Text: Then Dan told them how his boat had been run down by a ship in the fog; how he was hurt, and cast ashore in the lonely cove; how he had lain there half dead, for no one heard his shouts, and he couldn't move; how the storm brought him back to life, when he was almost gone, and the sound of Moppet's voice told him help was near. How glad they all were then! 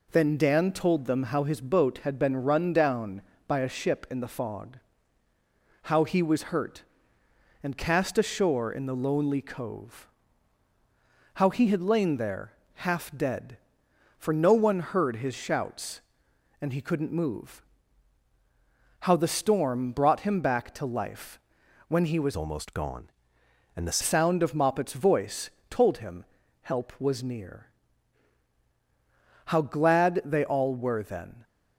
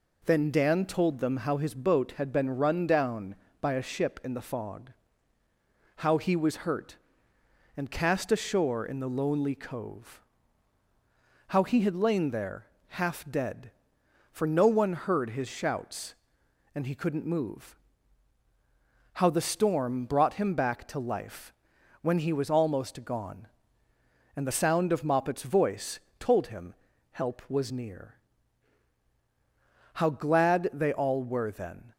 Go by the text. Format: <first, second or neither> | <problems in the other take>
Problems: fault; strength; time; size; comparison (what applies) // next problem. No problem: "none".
second | pauses between "there" and "half"; slight; at 12.5 s; 0.20 s long; slight in the second // changes voice from "almost" to "the"; from 22.3 to 23.9 s; 1.6 s long // pauses between "voice" and "told"; slight; at 25.4 s; 0.20 s long; slight in the second // pauses between "him" and "help"; at 26.2 s; 0.38 s long; also in the second